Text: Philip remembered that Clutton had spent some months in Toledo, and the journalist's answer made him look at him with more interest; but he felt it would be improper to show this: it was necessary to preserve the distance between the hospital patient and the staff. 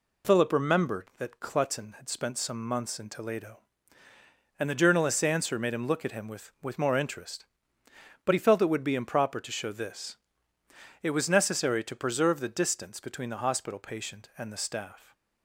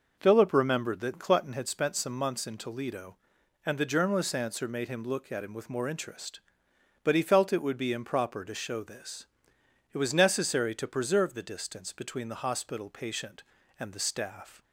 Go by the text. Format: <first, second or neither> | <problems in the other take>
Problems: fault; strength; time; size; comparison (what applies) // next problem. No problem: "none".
second | says "with" twice; at 6.6 s